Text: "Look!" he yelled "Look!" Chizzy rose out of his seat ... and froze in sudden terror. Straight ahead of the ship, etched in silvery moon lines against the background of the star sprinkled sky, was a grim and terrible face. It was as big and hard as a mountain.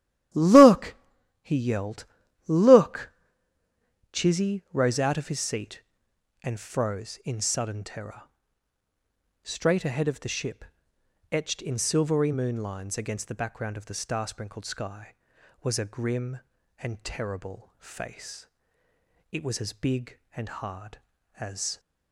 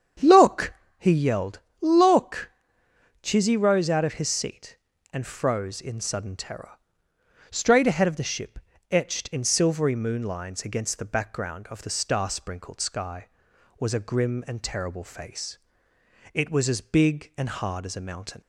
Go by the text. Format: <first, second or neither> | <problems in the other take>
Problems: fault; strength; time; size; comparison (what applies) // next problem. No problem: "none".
second | starts louder than the rest; strong; until 1.8 s; 12 dB; strong in the second // pauses between "yelled" and "Look"; at 2.0 s; 0.42 s long; slight in the second // stops before "a mountain"; at 21.7 s